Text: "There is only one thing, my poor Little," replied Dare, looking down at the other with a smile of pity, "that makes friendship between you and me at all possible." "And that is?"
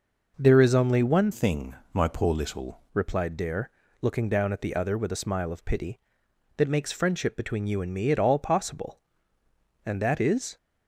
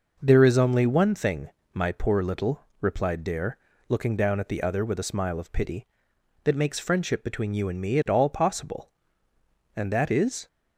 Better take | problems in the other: second | changes voice from "thing" to "Little"; from 1.3 to 2.8 s; 1.5 s long

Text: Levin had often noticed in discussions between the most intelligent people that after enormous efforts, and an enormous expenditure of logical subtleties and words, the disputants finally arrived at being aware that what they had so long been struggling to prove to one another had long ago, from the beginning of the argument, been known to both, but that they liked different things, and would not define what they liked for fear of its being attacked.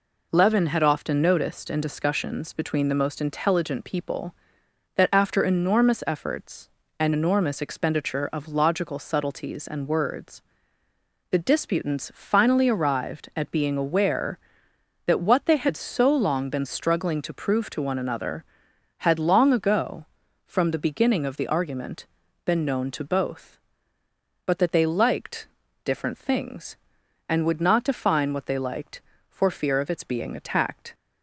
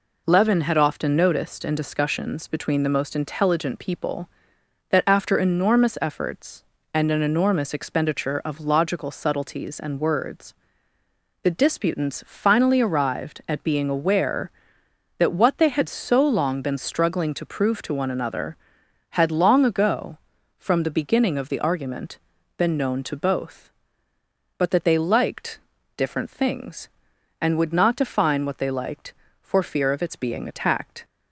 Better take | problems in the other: second | skips "an"; at 7.1 s // pauses between "liked" and "different"; at 25.4 s; 0.38 s long; also in the second

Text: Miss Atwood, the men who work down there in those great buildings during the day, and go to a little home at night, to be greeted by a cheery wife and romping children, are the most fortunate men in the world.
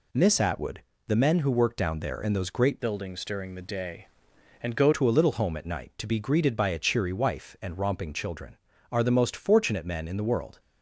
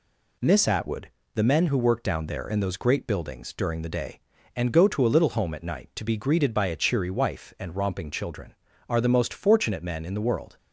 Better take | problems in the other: second | changes voice from "buildings" to "go"; from 2.7 to 4.9 s; 2.2 s long

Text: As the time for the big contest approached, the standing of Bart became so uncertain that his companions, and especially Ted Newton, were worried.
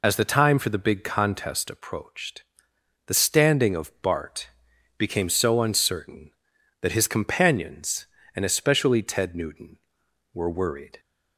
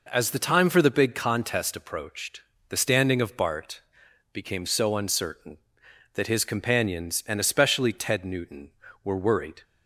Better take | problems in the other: second | loses the start of "As"; at 0.0 s; 40 ms // pauses between "Bart" and "became"; noticeable; at 4.4 s; 0.46 s long; noticeable in the second

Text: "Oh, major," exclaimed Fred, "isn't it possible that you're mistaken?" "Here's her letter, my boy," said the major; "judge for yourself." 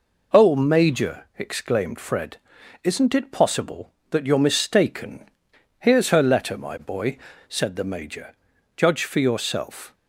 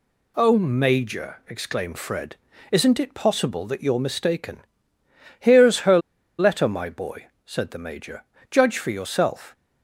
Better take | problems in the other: first | pauses between "her" and "letter"; at 5.9 s; 0.40 s long

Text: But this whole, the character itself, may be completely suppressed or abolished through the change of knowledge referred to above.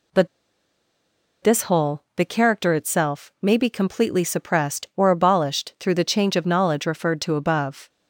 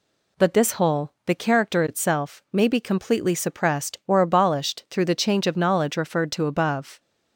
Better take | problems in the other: second | pauses between "But" and "this"; at 0.2 s; 1.1 s long

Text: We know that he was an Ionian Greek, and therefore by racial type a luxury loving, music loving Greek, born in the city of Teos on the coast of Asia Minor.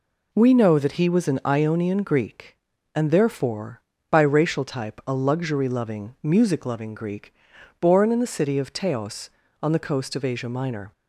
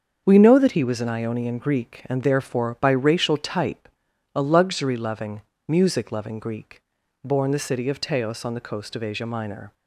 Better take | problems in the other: first | starts louder than the rest; until 1.2 s; 7 dB // pauses between "type" and "a"; noticeable; at 3.8 s; 0.46 s long // skips "in"; at 7.5 s

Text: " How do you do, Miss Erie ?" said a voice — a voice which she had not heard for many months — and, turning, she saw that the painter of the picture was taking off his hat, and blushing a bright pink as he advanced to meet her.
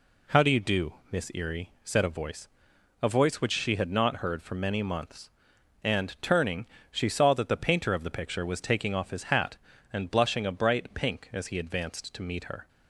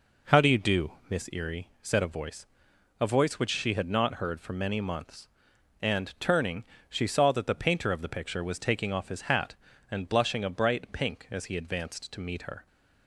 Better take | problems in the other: first | starts louder than the rest; noticeable; until 1.2 s; 4.5 dB

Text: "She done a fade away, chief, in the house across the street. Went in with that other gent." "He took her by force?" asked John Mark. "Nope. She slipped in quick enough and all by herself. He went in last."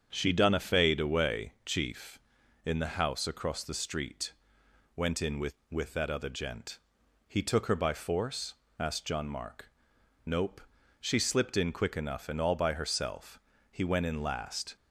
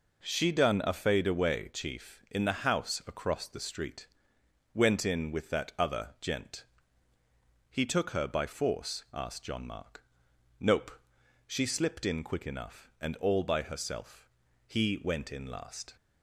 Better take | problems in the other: second | starts louder than the rest; strong; until 1.1 s; 7 dB // says "with" twice; at 5.7 s

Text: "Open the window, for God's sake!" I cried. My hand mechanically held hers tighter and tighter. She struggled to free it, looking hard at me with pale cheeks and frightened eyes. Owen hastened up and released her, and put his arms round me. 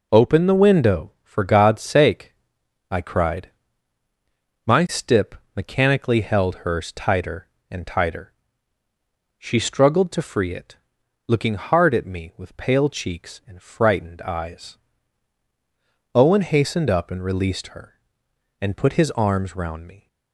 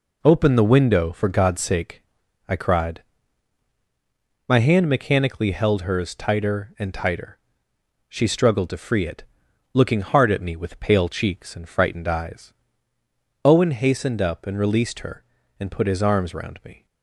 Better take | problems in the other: second | says "stip" for "hand"; at 4.8 s

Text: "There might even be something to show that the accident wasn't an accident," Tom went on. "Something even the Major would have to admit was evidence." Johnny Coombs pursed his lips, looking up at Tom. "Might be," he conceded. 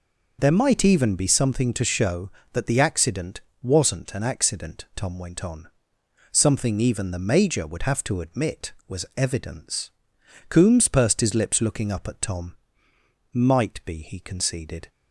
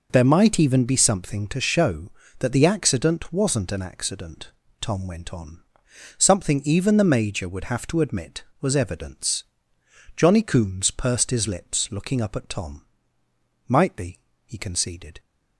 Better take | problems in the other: second | pauses between "accident" and "wasn't"; slight; at 3.4 s; 0.20 s long // skips "Johnny"; at 10.1 s

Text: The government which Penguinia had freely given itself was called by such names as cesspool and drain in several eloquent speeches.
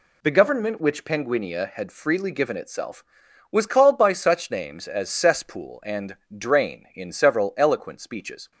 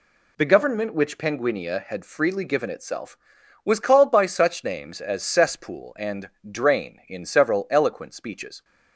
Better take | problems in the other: neither | pauses between "and" and "drain"; slight; the same in both

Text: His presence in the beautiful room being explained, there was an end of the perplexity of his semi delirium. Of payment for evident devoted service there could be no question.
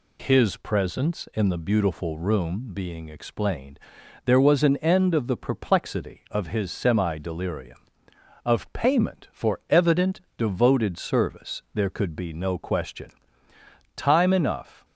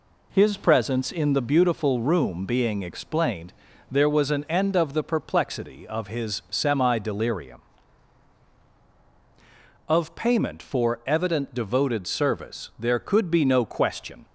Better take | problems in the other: second | pauses between "evident" and "devoted"; slight; at 10.2 s; 0.16 s long // goes on to say "Time enough"; noticeable; from 13.9 s on; 0.88 s long

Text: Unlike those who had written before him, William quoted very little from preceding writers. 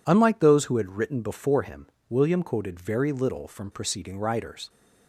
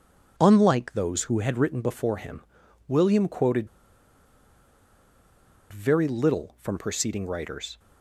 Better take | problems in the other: first | pauses between "quoted" and "very"; strong; at 3.6 s; 2.0 s long

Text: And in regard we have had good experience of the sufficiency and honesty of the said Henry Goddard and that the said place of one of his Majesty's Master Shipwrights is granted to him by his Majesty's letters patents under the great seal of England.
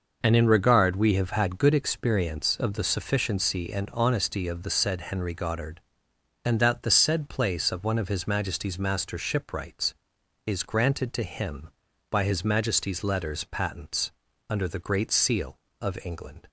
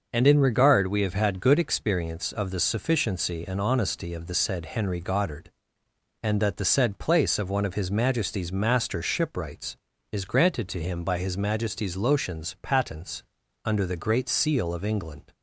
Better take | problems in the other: first | says "lotions" for "letters"; at 11.9 s // pauses between "patents" and "under"; at 13.2 s; 0.42 s long; also in the first

